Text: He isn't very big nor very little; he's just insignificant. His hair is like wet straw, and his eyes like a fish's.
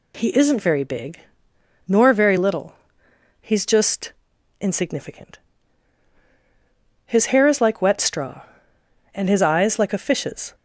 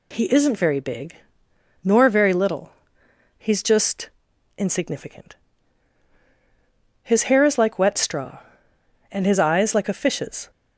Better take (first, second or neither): neither